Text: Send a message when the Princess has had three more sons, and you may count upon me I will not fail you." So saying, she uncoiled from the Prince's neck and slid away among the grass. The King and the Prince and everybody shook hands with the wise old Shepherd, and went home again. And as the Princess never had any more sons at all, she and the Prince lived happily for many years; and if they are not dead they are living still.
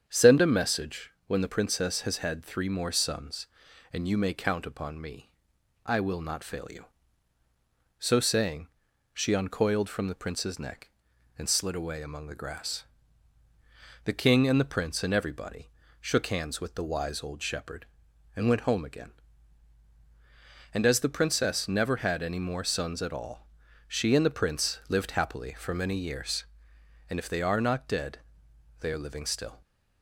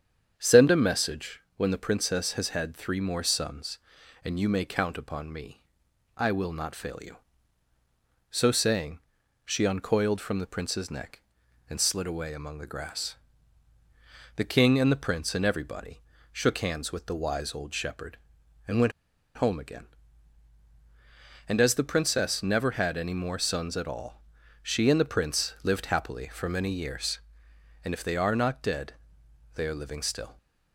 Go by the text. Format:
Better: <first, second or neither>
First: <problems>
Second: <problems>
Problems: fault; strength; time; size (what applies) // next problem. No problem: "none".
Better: first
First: starts louder than the rest; strong; until 1.0 s; 8 dB // pauses between "message" and "when"; slight; at 1.1 s; 0.16 s long // pauses between "me" and "I"; noticeable; at 5.3 s; 0.56 s long // pauses between "everybody" and "shook"; slight; at 15.6 s; 0.32 s long // pauses between "dead" and "they"; noticeable; at 28.1 s; 0.62 s long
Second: starts louder than the rest; strong; until 1.3 s; 8 dB // pauses between "message" and "when"; slight; at 1.3 s; 0.16 s long // pauses between "me" and "I"; noticeable; at 5.6 s; 0.56 s long // pauses between "everybody" and "shook"; slight; at 15.9 s; 0.32 s long // pauses between "went" and "home"; at 18.9 s; 0.45 s long // pauses between "dead" and "they"; noticeable; at 28.9 s; 0.62 s long